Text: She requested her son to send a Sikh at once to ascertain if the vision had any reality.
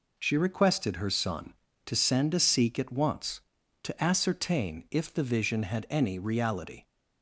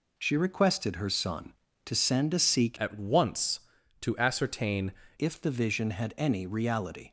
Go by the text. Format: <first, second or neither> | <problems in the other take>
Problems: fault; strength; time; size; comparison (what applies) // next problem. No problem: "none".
first | changes voice from "at" to "ascertain"; from 2.7 to 4.9 s; 2.2 s long